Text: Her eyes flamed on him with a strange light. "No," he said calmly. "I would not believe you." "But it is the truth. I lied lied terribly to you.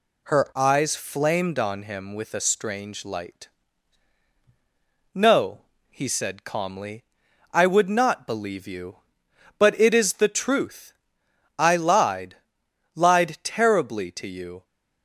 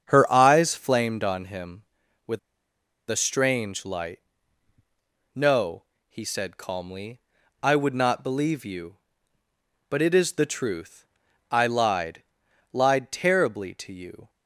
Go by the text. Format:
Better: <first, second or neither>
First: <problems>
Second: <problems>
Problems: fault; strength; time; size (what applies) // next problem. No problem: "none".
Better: first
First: pauses between "lied" and "lied"; noticeable; at 12.3 s; 0.60 s long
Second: starts louder than the rest; strong; until 1.0 s; 7.5 dB // pauses between "with" and "a"; noticeable; at 2.3 s; 0.70 s long // pauses between "lied" and "lied"; noticeable; at 12.2 s; 0.50 s long